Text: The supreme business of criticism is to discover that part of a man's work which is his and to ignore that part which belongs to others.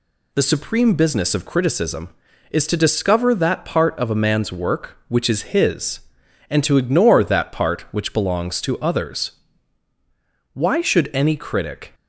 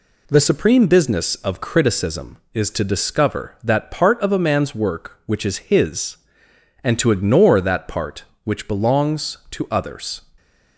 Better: second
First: goes on to say "Why should any critic"; from 10.5 s on; 1.4 s long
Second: none

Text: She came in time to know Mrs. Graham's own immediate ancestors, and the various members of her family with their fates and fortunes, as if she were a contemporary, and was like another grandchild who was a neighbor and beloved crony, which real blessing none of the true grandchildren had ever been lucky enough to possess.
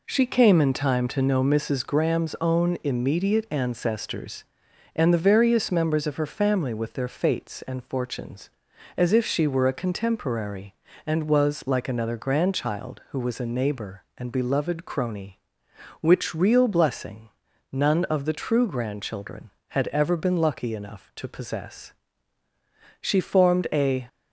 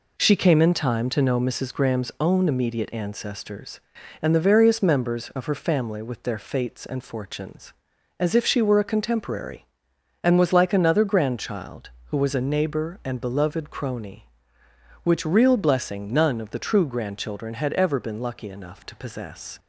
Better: second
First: pauses between "blessing" and "none"; at 17.2 s; 0.42 s long // goes on to say "She formed a"; noticeable; from 23.0 s on; 1.0 s long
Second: none

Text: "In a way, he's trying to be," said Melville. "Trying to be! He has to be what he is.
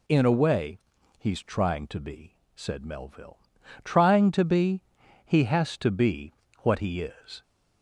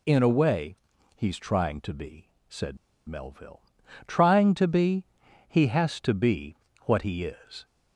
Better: first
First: pauses between "be" and "what"; slight; at 6.3 s; 0.30 s long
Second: pauses between "said" and "Melville"; slight; at 2.7 s; 0.32 s long // pauses between "be" and "what"; slight; at 6.5 s; 0.30 s long

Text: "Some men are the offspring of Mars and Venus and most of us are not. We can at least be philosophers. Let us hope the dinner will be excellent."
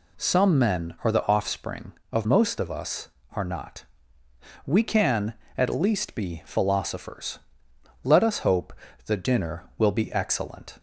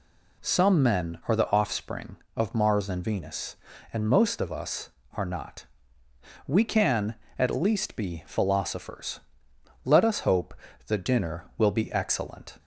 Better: second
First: skips "Mars and Venus and"; at 2.2 s // pauses between "hope" and "the"; slight; at 8.7 s; 0.32 s long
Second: pauses between "hope" and "the"; slight; at 10.5 s; 0.32 s long

